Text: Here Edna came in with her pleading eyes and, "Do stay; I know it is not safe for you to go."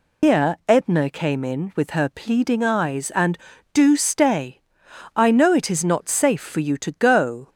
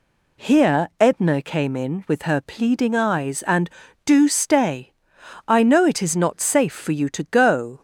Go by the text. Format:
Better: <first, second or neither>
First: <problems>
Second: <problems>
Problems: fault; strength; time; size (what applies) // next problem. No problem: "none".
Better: second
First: loses the start of "Here"; at 0.2 s; 145 ms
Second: none